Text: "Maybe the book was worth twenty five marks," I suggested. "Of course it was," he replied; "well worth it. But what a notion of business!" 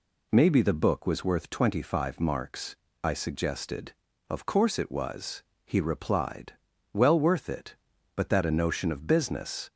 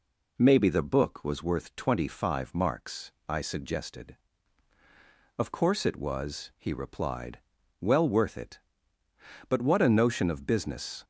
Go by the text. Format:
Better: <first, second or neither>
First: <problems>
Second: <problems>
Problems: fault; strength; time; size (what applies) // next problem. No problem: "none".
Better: second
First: says "that" for "what"; at 8.2 s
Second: none